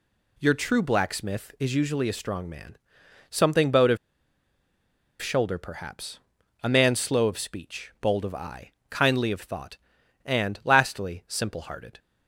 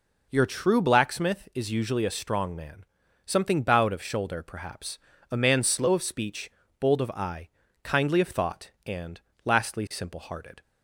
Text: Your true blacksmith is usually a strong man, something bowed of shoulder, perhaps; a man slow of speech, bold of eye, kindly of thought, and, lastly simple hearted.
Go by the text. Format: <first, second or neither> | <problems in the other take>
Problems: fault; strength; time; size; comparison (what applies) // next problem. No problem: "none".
second | pauses between "of" and "shoulder"; at 3.9 s; 1.2 s long